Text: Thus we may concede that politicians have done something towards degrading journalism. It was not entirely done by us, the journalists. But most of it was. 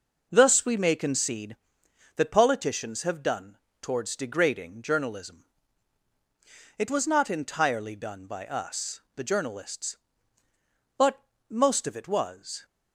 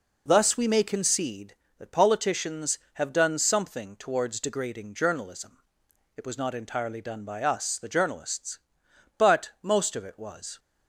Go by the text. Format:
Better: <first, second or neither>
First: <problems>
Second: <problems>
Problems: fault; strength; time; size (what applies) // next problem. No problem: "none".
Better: second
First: skips "something"; at 3.6 s // pauses between "But" and "most"; slight; at 11.1 s; 0.30 s long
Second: none